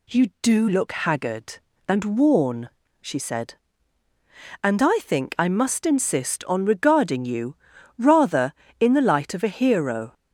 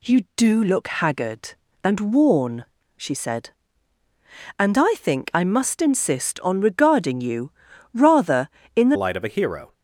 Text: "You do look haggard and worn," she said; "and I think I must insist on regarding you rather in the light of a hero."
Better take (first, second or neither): first